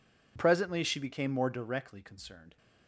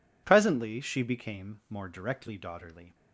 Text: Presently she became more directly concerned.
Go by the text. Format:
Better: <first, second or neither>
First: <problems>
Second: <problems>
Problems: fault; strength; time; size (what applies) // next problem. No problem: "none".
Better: first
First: none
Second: says "daughterly" for "concerned"; at 2.3 s